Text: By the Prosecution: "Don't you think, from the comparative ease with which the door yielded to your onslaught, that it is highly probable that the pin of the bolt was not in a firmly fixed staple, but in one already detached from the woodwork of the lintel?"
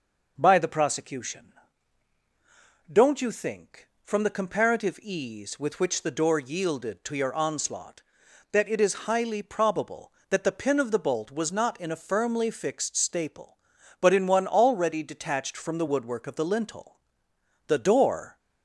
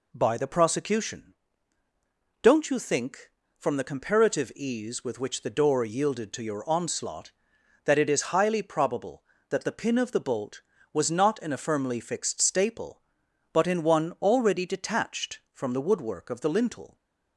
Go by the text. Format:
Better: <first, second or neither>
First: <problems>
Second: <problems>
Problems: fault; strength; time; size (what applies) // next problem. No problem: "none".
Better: second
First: goes on to say "The door"; noticeable; from 17.6 s on; 0.72 s long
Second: none